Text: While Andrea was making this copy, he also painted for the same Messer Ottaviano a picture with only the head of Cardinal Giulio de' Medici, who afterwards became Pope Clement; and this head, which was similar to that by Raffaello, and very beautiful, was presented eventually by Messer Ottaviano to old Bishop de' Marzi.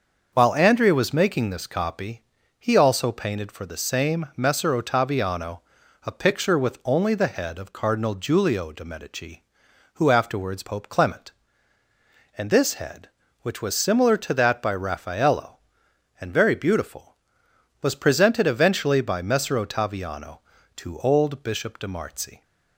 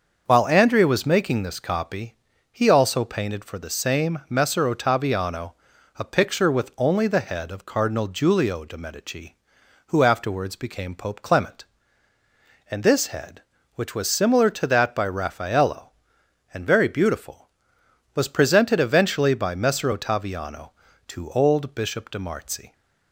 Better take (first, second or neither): second